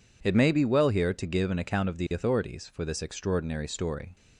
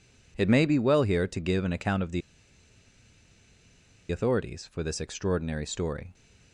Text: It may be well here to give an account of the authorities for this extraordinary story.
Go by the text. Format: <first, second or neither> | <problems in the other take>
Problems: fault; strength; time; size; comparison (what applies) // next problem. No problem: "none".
first | pauses between "the" and "authorities"; strong; at 2.2 s; 1.9 s long